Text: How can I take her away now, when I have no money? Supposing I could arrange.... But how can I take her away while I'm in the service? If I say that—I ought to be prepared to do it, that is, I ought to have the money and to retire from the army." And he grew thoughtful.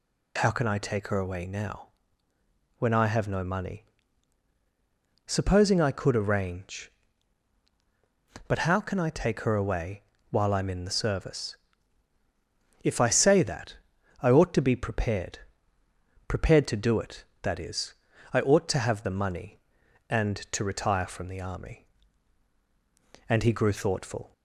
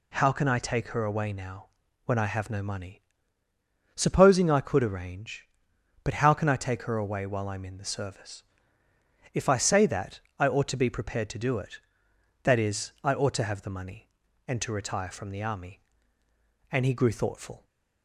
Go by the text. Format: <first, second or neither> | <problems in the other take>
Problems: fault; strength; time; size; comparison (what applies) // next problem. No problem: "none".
second | pauses between "away" and "while"; slight; at 10.0 s; 0.28 s long // says "prepared" twice; at 16.2 s